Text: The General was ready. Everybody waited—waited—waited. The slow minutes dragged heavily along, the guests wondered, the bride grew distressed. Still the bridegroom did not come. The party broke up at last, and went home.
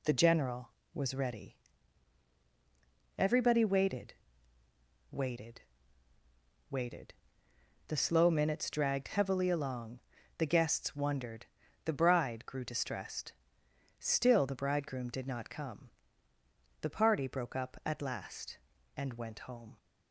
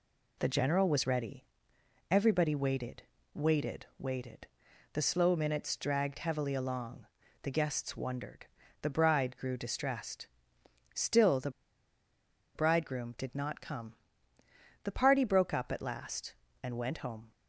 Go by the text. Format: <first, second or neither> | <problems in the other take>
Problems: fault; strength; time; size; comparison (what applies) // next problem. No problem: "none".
first | pauses between "the" and "bridegroom"; at 11.4 s; 1.0 s long